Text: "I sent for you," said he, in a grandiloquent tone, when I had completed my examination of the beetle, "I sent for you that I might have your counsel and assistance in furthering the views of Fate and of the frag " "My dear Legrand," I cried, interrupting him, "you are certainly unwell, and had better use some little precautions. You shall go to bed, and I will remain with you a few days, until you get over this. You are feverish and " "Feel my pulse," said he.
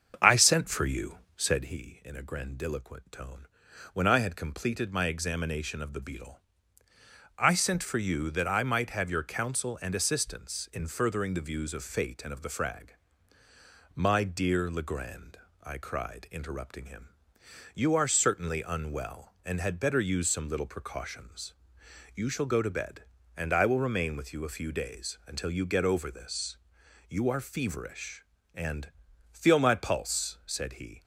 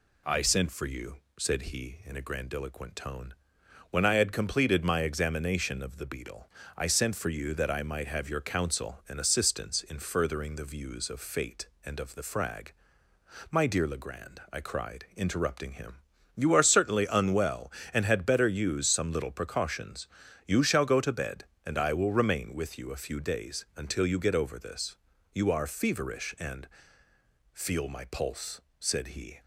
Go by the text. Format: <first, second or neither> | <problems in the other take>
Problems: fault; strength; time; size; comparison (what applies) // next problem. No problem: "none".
second | starts louder than the rest; until 1.8 s; 7 dB